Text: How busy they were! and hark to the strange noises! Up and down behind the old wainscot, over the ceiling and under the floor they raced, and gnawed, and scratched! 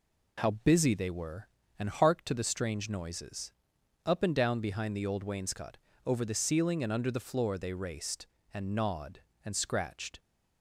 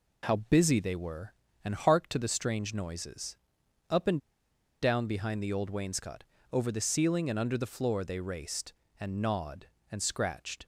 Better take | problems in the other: first | pauses between "and" and "down"; noticeable; at 4.1 s; 0.64 s long

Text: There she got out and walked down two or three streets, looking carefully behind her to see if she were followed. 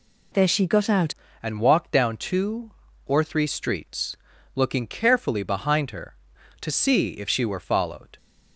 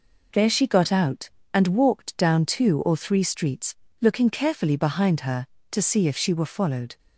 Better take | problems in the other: second | changes voice at "and"; from 1.4 s on; 6.7 s long

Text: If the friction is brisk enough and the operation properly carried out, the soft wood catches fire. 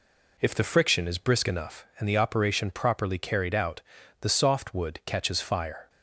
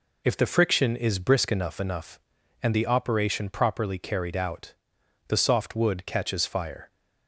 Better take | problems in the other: first | says "enough" twice; at 1.7 s

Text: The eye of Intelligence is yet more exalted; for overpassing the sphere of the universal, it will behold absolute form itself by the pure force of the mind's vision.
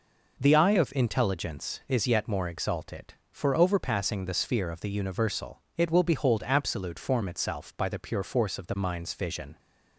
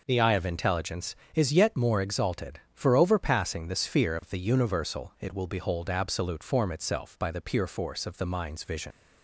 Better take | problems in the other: first | leaves "vision" unfinished; at 8.9 s; 90 ms

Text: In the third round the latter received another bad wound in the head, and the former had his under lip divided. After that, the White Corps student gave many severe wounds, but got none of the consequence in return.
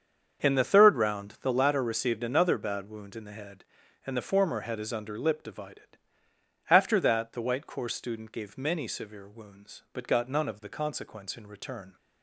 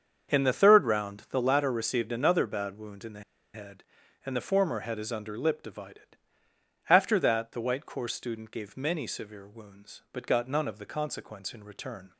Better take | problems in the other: first | starts louder than the rest; until 1.4 s; 7 dB; also in the first // pauses between "the" and "head"; slight; at 3.2 s; 0.32 s long

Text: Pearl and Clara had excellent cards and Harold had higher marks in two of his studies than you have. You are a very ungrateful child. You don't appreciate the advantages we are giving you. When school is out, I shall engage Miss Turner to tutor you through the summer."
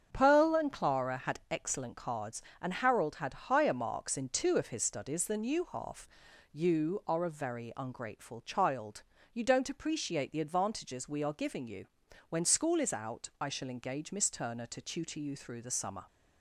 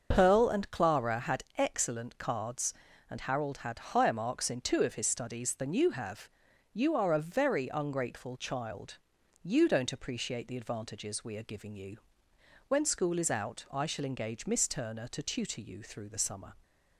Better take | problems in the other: second | starts louder than the rest; strong; until 1.1 s; 7.5 dB; also in the second // says "half" for "have"; at 5.7 s

